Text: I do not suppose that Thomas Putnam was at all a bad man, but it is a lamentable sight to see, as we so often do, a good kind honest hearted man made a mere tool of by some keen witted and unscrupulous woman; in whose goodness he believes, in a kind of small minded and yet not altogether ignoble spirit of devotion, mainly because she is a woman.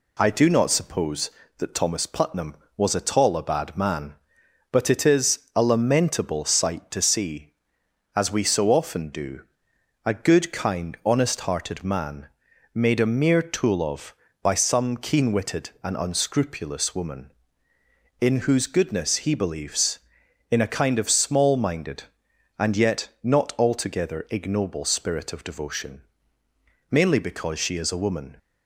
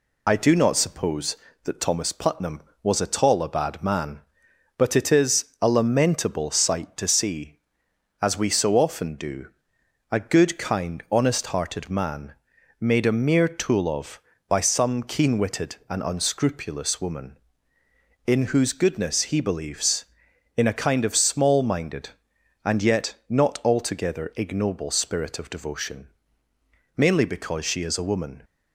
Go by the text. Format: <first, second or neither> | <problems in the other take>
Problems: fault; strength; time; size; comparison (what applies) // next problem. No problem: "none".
first | loses the start of "I"; at 0.2 s; 40 ms // pauses between "is" and "a"; slight; at 5.4 s; 0.16 s long; slight in the first // pauses between "man" and "made"; noticeable; at 12.3 s; 0.48 s long; noticeable in the first